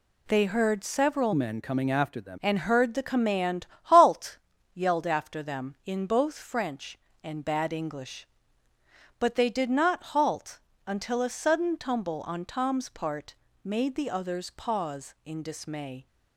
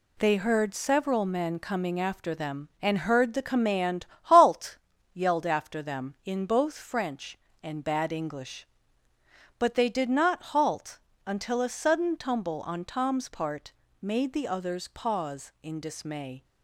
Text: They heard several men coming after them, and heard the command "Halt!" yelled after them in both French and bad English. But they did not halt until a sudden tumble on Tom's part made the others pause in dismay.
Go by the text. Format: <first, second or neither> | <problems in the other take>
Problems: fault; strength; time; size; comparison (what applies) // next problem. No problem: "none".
second | changes voice from "men" to "them"; from 1.3 to 2.3 s; 1.0 s long // pauses between "command" and "Halt"; slight; at 3.6 s; 0.16 s long; slight in the second // pauses between "halt" and "until"; slight; at 10.5 s; 0.30 s long; slight in the second // pauses between "part" and "made"; slight; at 13.3 s; 0.28 s long; slight in the second